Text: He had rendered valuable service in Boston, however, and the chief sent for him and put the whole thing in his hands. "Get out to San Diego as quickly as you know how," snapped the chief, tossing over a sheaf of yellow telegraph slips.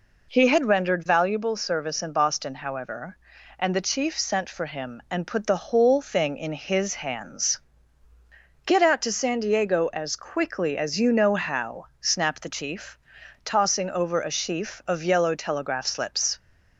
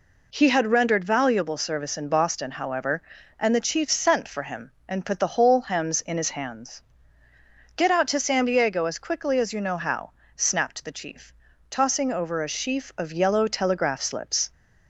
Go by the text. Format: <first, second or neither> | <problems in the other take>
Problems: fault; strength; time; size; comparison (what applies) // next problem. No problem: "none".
first | says "hems" for "thing"; at 5.6 s